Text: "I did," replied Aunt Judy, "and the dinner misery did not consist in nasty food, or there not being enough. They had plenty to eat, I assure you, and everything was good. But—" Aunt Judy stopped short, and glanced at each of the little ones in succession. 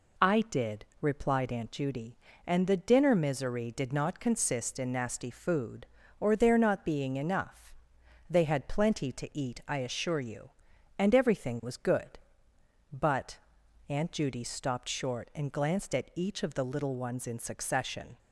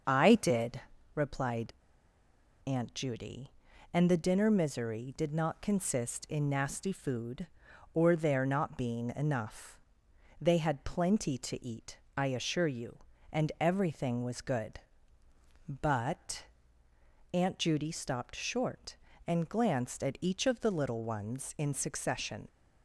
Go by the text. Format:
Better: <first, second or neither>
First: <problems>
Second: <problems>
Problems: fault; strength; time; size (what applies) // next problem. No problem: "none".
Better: first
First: none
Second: starts louder than the rest; until 1.3 s; 6.5 dB // pauses between "replied" and "Aunt"; noticeable; at 1.7 s; 0.92 s long